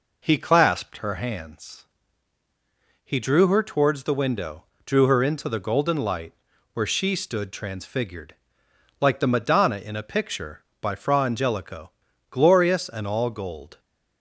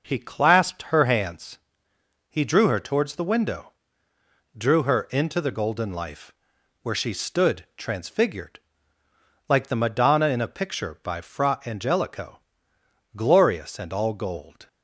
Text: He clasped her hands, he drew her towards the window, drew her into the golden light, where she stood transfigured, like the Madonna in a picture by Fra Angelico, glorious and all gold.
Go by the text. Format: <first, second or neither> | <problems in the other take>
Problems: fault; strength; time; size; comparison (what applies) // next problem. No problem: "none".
first | says "life" for "light"; at 5.9 s